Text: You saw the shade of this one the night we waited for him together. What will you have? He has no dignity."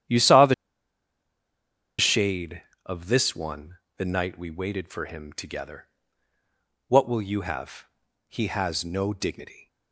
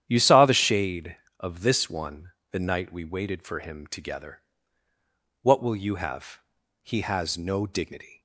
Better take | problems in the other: second | starts louder than the rest; strong; until 2.5 s; 10 dB; strong in the second // pauses between "the" and "shade"; strong; at 0.5 s; 1.4 s long // pauses between "one" and "the"; slight; at 3.7 s; 0.22 s long; slight in the second

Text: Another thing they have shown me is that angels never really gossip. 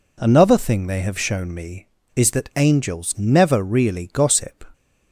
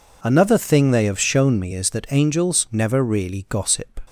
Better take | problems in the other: neither | none

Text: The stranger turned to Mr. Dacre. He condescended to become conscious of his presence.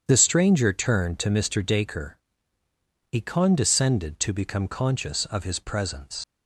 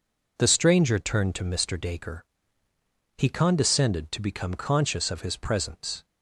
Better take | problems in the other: second | starts louder than the rest; strong; until 1.0 s; 8 dB // leaves "presence" unfinished; at 6.2 s; 65 ms

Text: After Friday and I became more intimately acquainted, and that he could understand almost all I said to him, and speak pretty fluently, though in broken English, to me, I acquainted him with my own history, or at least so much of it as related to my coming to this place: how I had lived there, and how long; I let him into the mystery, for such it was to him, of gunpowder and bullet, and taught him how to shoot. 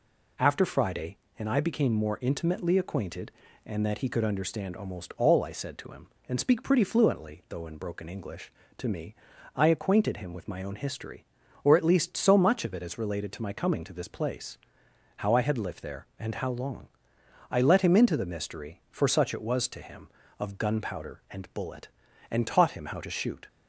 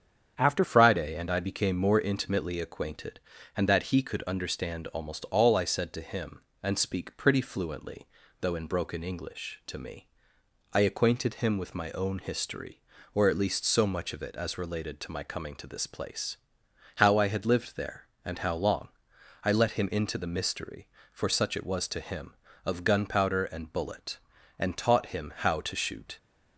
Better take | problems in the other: first | starts louder than the rest; strong; until 1.3 s; 8 dB // changes voice at "Friday"; from 0.6 s on; 25.5 s long

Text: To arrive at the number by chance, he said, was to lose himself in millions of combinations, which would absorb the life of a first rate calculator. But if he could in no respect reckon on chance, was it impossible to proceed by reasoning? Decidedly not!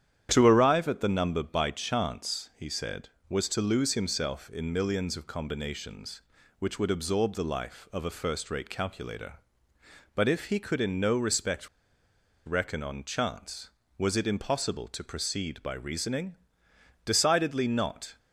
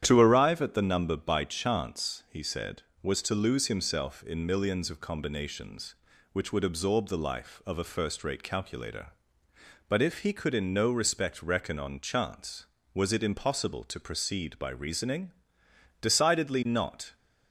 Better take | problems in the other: second | starts louder than the rest; strong; until 1.3 s; 9.5 dB; strong in the second // pauses between "respect" and "reckon"; noticeable; at 11.6 s; 0.77 s long

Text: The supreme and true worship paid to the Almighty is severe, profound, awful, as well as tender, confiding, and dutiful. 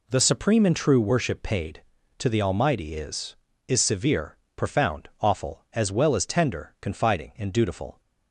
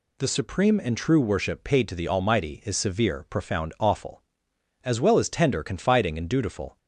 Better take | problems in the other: second | says "is" twice; at 3.6 s

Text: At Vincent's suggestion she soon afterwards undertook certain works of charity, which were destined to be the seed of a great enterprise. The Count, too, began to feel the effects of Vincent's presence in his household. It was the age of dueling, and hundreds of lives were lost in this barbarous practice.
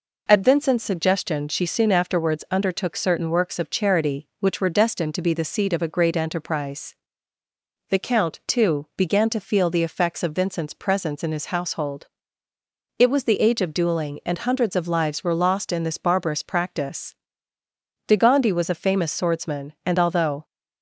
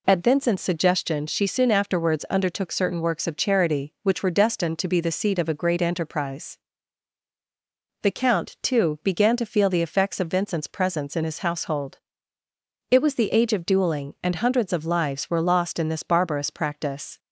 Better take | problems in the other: second | goes on to say "De Gondi was a famous swordsman and although"; strong; from 18.0 s on; 2.3 s long

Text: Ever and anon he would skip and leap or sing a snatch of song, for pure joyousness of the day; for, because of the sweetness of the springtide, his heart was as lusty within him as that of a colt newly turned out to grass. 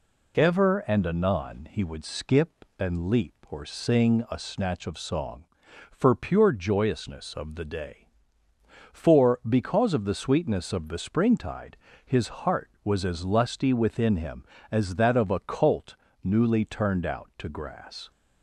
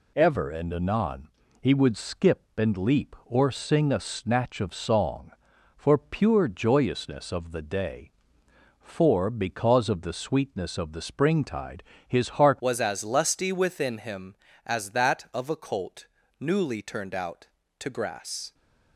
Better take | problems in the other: first | pauses between "anon" and "he"; slight; at 1.2 s; 0.32 s long // changes voice at "was"; from 12.5 s on; 6.0 s long // pauses between "colt" and "newly"; slight; at 16.0 s; 0.34 s long; slight in the first

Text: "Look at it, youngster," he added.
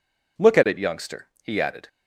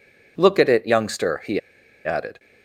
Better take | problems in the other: first | pauses between "he" and "added"; noticeable; at 1.5 s; 0.46 s long

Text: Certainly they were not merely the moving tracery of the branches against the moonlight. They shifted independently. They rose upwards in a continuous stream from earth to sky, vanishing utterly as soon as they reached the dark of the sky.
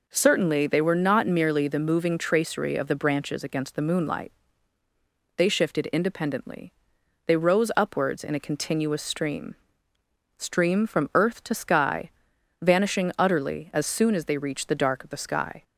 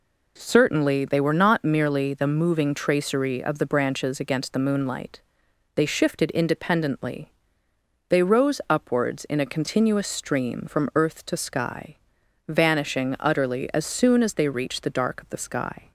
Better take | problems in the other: second | says "stream" twice; at 10.3 s

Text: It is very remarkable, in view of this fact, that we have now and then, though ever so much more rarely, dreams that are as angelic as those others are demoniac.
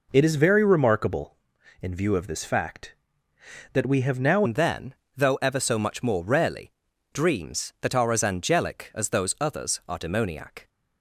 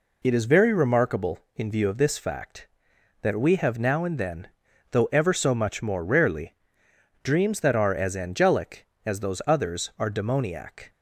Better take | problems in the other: second | changes voice at "and"; from 4.4 s on; 6.2 s long

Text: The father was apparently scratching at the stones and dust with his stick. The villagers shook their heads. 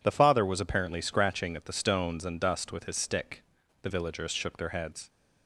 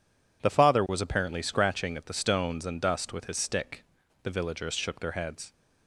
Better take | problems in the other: neither | none

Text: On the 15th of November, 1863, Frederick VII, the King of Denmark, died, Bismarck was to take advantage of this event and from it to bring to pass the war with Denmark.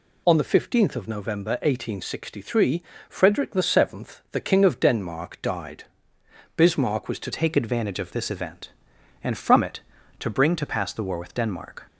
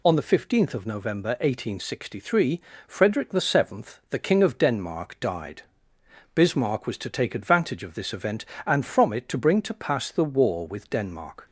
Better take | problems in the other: second | changes voice at "take"; from 7.3 s on; 4.5 s long

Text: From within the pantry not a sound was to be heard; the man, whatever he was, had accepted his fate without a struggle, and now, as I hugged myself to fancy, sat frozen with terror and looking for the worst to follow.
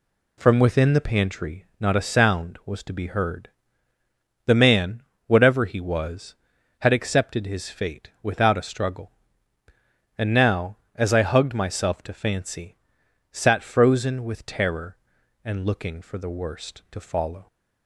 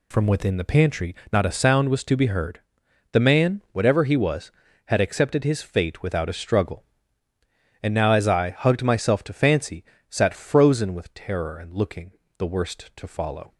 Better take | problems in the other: first | pauses between "pantry" and "not"; slight; at 1.1 s; 0.16 s long; slight in the first // skips "for"; at 12.2 s

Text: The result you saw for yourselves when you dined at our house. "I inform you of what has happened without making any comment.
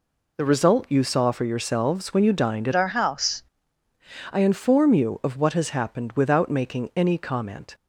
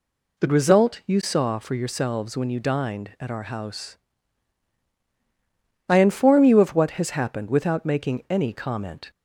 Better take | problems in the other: second | changes voice from "our" to "house"; from 2.7 to 3.4 s; 0.7 s long

